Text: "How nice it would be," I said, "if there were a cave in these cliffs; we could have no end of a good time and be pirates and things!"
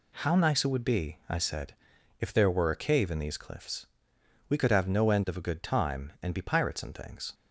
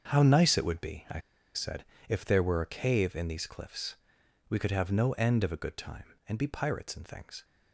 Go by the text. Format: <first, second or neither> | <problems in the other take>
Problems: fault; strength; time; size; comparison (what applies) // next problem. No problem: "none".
first | starts louder than the rest; until 1.1 s; 6.5 dB // pauses between "I" and "said"; at 1.1 s; 0.36 s long